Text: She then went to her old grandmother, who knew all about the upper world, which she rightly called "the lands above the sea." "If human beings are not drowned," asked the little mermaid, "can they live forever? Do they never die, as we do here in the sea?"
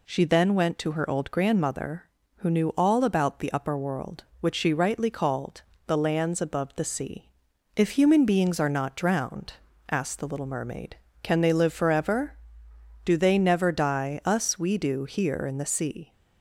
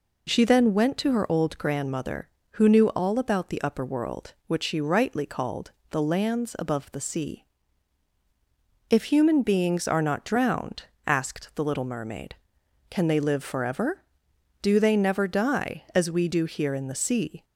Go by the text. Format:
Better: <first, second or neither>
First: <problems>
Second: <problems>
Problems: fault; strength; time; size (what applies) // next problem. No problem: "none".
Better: second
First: pauses between "called" and "the"; slight; at 5.6 s; 0.26 s long // says "us" for "as"; at 14.2 s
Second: pauses between "called" and "the"; slight; at 5.7 s; 0.16 s long